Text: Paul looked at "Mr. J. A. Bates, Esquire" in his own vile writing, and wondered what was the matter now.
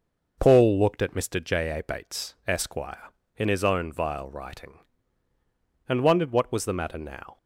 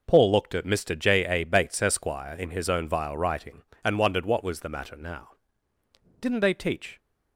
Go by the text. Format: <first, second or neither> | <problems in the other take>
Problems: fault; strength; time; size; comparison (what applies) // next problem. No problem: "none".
first | goes on to say "Didn't they teach"; noticeable; from 6.2 s on; 0.78 s long